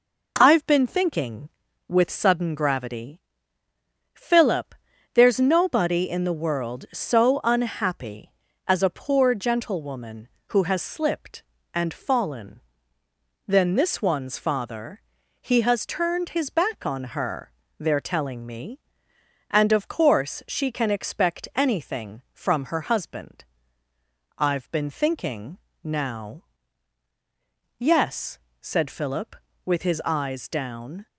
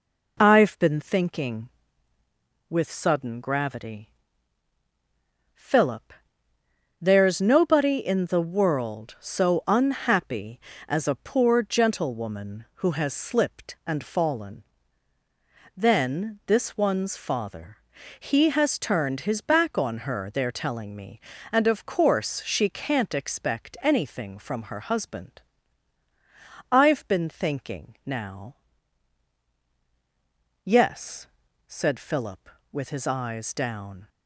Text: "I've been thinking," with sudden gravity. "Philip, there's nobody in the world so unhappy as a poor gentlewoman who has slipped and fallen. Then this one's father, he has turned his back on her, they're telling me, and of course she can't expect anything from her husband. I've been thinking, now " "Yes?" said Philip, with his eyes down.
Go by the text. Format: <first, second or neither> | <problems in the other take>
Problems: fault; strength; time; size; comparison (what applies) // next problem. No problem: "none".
second | says "can" for "can't"; at 20.7 s